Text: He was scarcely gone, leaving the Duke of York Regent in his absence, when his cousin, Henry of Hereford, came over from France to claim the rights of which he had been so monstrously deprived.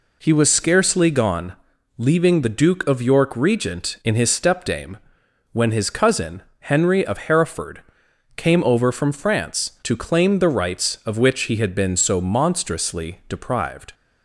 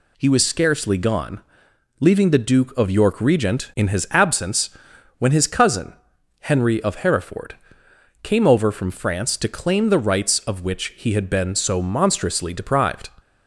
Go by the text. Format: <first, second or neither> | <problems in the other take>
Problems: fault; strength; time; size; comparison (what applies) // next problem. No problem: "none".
second | says "stepdame" for "absence"; at 4.2 s